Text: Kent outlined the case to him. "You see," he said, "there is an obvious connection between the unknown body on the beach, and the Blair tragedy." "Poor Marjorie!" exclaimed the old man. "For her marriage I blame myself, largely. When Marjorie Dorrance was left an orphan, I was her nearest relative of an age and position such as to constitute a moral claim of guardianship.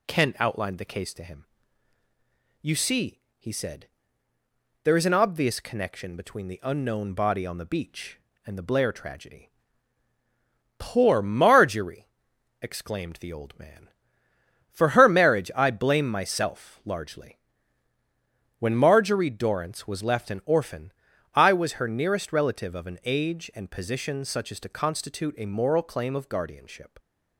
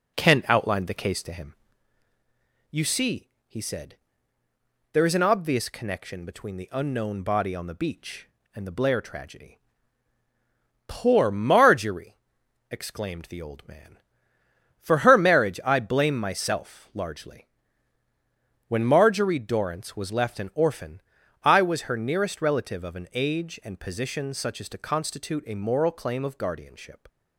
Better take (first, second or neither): first